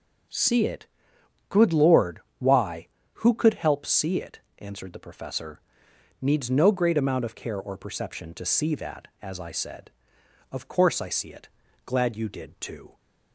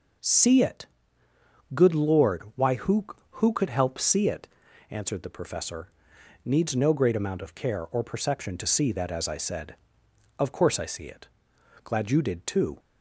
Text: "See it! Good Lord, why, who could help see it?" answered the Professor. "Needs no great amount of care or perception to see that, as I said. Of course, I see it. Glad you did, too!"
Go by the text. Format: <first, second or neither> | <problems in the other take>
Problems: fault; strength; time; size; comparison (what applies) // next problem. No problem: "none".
first | says "who" twice; at 3.3 s